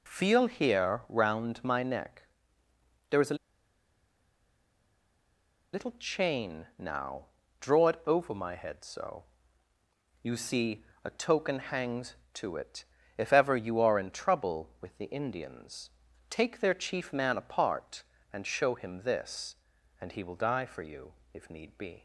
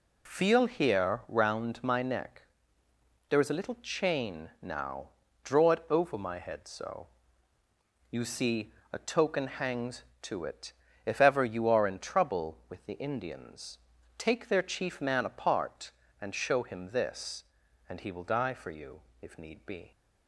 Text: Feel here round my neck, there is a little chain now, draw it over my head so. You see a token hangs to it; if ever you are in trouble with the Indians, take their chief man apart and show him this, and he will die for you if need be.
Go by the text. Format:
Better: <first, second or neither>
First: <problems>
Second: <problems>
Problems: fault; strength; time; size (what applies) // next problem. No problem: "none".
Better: second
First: pauses between "a" and "little"; strong; at 3.3 s; 2.3 s long // pauses between "see" and "a"; slight; at 10.8 s; 0.20 s long // pauses between "you" and "if"; slight; at 21.1 s; 0.20 s long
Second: pauses between "see" and "a"; slight; at 8.7 s; 0.20 s long // pauses between "you" and "if"; slight; at 19.0 s; 0.20 s long